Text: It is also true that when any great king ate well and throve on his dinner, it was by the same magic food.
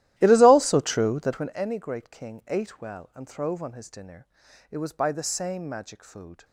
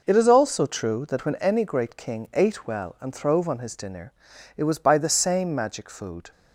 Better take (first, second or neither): second